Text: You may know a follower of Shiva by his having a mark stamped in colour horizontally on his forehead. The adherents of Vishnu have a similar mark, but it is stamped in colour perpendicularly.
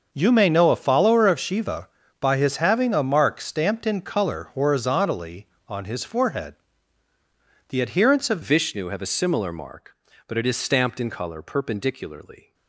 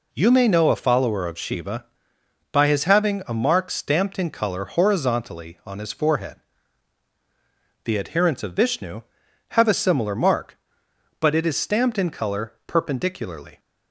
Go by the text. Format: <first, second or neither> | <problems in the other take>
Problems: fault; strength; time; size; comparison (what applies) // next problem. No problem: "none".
second | starts louder than the rest; noticeable; until 1.1 s; 6 dB // changes voice at "Vishnu"; from 8.4 s on; 4.1 s long